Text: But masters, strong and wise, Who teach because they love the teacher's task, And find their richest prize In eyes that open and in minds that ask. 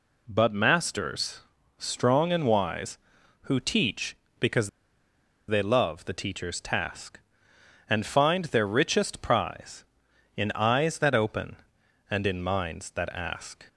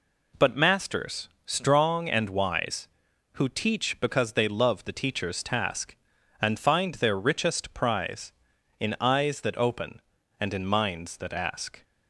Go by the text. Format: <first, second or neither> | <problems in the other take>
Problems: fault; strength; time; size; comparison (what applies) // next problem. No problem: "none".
second | pauses between "because" and "they"; noticeable; at 4.6 s; 0.79 s long